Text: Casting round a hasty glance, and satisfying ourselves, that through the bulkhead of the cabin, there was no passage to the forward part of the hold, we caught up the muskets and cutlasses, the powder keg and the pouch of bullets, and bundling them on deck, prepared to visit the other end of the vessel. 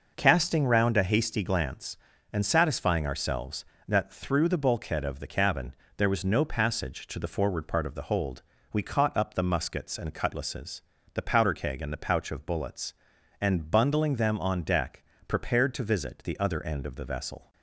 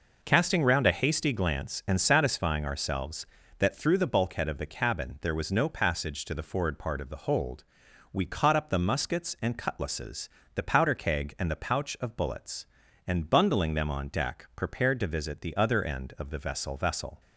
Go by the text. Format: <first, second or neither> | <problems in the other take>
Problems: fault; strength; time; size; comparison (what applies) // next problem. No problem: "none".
first | says "vessel" twice; at 16.7 s